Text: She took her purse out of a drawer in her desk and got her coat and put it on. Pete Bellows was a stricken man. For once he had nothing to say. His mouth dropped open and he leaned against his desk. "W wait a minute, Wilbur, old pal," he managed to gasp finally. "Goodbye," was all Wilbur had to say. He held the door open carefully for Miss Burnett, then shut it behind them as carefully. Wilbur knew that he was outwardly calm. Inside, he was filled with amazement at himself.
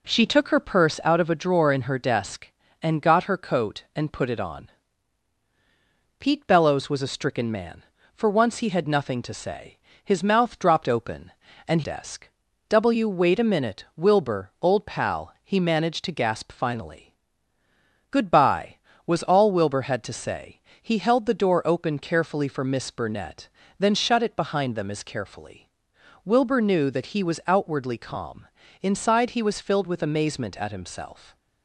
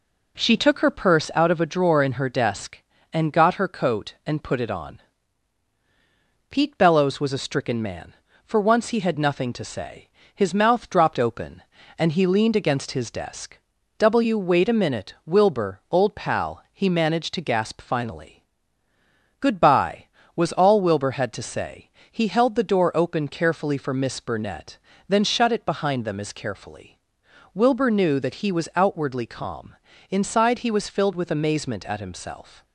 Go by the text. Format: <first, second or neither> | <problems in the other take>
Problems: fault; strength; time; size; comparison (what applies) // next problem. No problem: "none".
second | skips "he leaned against his"; at 11.8 s